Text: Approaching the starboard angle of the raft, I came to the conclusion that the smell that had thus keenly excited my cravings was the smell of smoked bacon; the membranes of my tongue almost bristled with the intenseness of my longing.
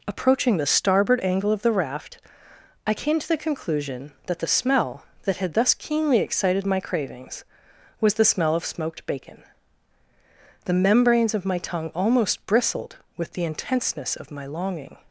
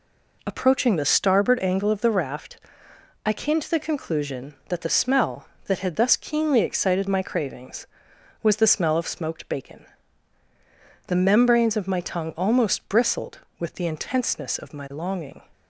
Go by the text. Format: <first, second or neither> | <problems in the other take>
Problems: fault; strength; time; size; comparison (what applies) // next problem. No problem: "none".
neither | none